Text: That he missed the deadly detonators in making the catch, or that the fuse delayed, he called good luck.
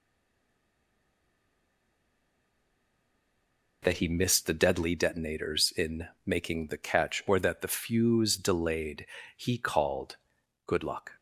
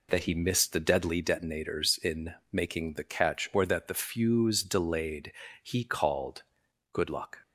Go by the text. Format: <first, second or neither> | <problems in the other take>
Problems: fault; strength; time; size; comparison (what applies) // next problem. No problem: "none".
second | stays silent before the first word; strong; until 3.8 s; 3.8 s long // pauses between "in" and "making"; slight; at 6.0 s; 0.18 s long; slight in the second // pauses between "called" and "good"; noticeable; at 10.1 s; 0.50 s long; noticeable in the second